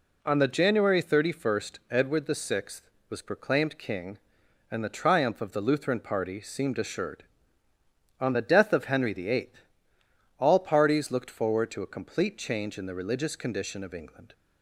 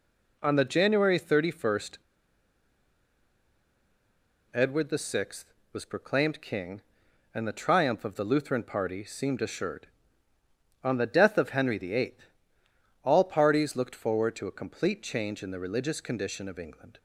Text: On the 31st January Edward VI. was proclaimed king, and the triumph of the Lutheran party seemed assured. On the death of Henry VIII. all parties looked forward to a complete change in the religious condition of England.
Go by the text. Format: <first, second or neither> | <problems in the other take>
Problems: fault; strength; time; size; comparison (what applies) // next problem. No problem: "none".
first | pauses between "January" and "Edward"; strong; at 1.9 s; 2.5 s long